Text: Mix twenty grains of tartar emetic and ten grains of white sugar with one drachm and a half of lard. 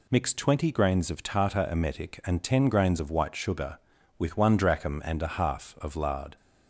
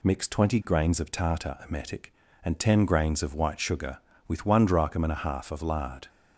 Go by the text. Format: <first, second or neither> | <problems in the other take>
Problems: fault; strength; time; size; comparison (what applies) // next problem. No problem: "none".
neither | none